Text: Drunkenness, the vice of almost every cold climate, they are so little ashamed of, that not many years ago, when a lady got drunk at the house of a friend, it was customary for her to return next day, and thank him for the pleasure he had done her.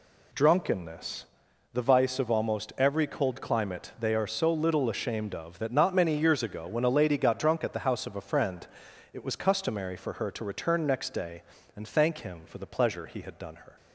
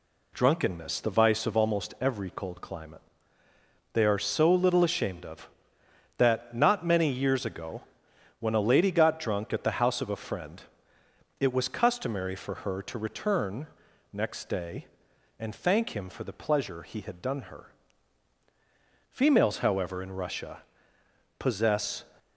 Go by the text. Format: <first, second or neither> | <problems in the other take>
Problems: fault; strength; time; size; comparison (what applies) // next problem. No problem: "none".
first | pauses between "return" and "next"; at 13.6 s; 0.44 s long // goes on to say "Females however in Russia possess"; strong; from 19.1 s on; 2.9 s long